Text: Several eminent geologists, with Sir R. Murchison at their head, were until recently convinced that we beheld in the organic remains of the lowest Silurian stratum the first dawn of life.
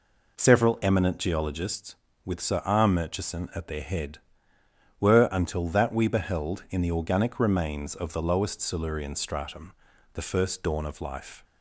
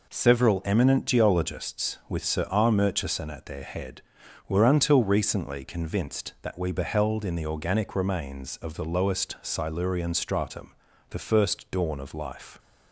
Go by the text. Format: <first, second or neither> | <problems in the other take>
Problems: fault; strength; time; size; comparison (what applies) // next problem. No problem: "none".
second | skips "recently convinced"; at 5.6 s // pauses between "stratum" and "the"; at 9.7 s; 0.40 s long; also in the second